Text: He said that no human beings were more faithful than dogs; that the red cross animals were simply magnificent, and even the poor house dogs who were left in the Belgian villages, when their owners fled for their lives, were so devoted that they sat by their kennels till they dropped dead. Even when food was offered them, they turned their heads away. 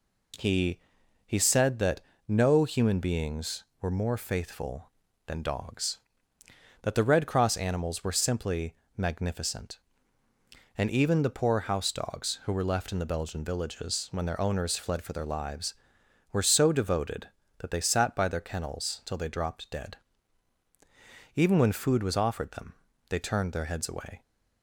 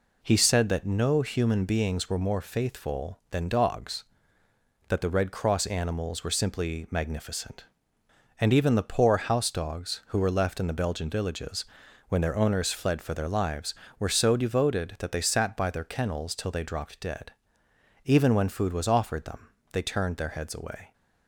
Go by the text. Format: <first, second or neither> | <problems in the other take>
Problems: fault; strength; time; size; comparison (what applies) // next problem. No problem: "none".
second | says "He" twice; at 1.2 s // pauses between "that" and "no"; slight; at 2.0 s; 0.26 s long // pauses between "simply" and "magnificent"; slight; at 8.7 s; 0.22 s long